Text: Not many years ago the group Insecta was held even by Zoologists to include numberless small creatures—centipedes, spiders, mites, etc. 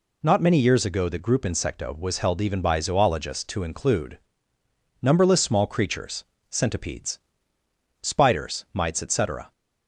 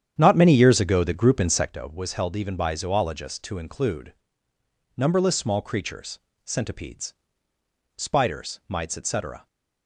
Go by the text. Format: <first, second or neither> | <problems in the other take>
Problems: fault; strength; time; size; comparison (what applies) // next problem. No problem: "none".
first | starts louder than the rest; strong; until 1.7 s; 9 dB // pauses between "include" and "numberless"; noticeable; at 4.1 s; 0.82 s long; noticeable in the first